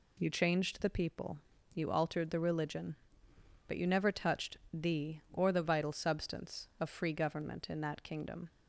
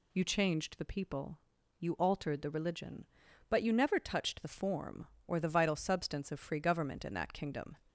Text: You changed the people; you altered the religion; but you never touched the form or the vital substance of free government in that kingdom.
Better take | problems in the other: second | pauses between "touched" and "the"; slight; at 4.5 s; 0.16 s long // skips "form"; at 5.2 s

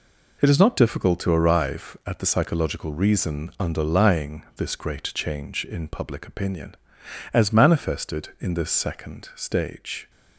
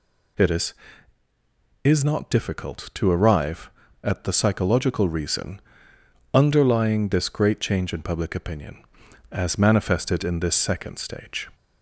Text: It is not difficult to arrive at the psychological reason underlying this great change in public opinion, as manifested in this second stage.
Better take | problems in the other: first | says "is" twice; at 1.8 s // pauses between "reason" and "underlying"; noticeable; at 5.6 s; 0.72 s long

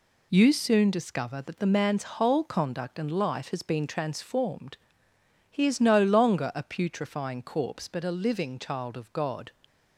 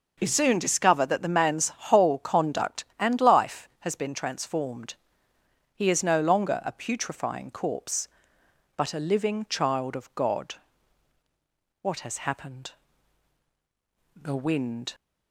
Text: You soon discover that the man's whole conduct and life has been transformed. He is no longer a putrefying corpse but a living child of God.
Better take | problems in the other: first | goes on to say "What has happened The Wind"; strong; from 11.8 s on; 3.1 s long

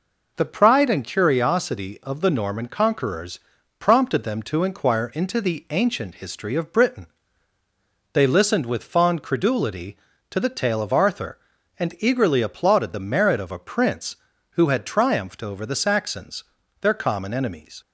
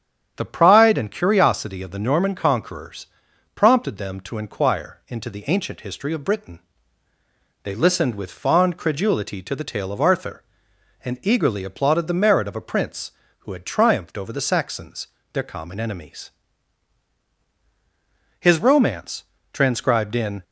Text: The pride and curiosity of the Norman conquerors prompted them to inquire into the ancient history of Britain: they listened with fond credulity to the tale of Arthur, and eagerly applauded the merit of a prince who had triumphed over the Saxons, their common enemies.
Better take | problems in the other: first | starts louder than the rest; strong; until 1.3 s; 9 dB // pauses between "conquerors" and "prompted"; noticeable; at 3.0 s; 0.48 s long; also in the first // goes on to say "His romance transcribed in"; strong; from 18.4 s on; 2.0 s long

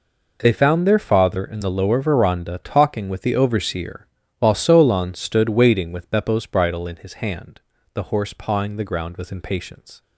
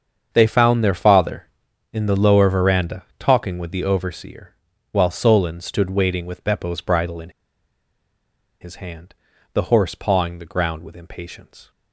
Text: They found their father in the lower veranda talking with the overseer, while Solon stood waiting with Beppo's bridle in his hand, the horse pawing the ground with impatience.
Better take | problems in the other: first | starts louder than the rest; strong; until 1.3 s; 7.5 dB // pauses between "veranda" and "talking"; slight; at 3.0 s; 0.16 s long // pauses between "in" and "his"; strong; at 7.2 s; 1.3 s long

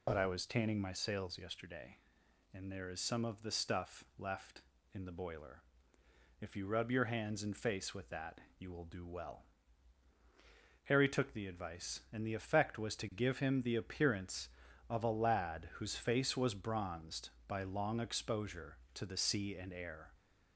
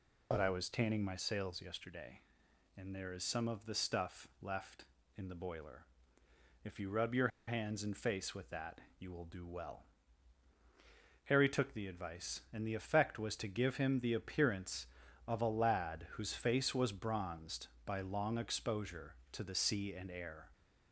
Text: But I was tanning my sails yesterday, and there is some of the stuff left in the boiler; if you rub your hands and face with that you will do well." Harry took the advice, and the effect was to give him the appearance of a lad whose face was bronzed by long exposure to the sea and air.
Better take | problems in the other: first | pauses between "your" and "hands"; slight; at 7.2 s; 0.19 s long // pauses between "that" and "you"; slight; at 8.7 s; 0.20 s long; slight in the first

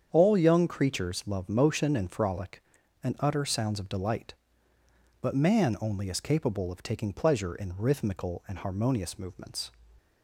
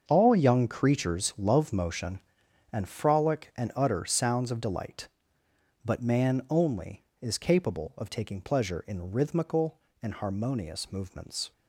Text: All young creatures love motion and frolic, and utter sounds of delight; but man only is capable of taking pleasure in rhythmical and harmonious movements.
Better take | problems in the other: first | gets quieter; strong; throughout; 12.5 dB // starts louder than the rest; until 1.0 s; 7 dB; strong in the first

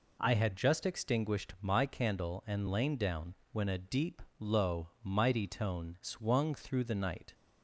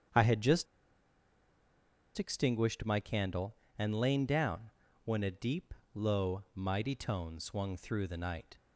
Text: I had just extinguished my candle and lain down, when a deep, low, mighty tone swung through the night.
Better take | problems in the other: first | starts louder than the rest; strong; until 2.6 s; 8 dB // pauses between "just" and "extinguished"; strong; at 0.6 s; 1.5 s long

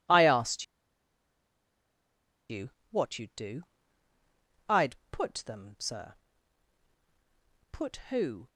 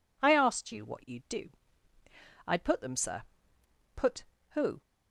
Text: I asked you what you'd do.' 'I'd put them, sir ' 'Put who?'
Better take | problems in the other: second | pauses between "asked" and "you"; strong; at 0.6 s; 1.8 s long // pauses between "you" and "what"; slight; at 2.6 s; 0.22 s long

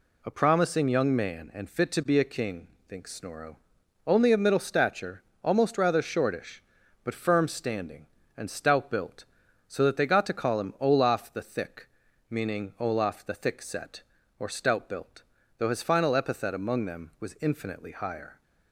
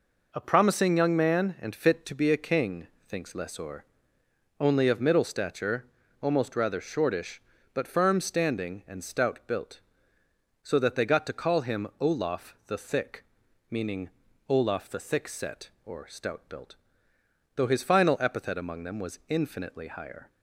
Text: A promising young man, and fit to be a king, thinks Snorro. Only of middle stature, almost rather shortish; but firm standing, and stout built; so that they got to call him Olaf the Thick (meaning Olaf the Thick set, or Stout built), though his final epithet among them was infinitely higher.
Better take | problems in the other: first | says "Lessor" for "Snorro"; at 3.3 s // pauses between "meaning" and "Olaf"; slight; at 14.1 s; 0.36 s long

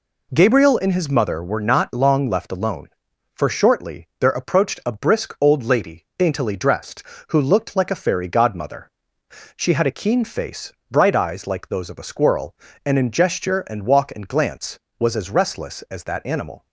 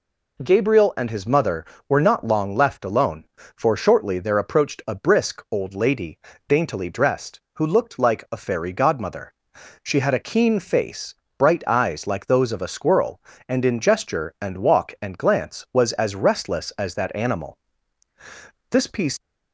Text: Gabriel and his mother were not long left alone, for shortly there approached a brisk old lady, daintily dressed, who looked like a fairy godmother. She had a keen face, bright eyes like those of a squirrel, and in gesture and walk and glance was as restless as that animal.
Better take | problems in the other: first | goes on to say "This piece"; slight; from 18.7 s on; 0.48 s long

